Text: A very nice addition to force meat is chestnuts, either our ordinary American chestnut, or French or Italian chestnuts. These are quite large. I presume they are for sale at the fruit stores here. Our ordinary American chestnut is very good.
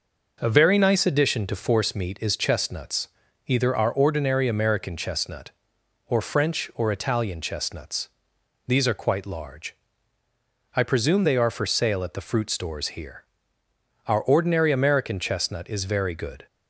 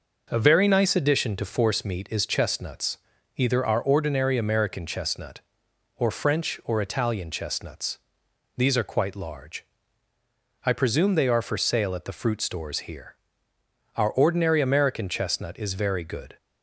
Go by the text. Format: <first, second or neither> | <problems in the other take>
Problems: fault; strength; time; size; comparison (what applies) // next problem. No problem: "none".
neither | none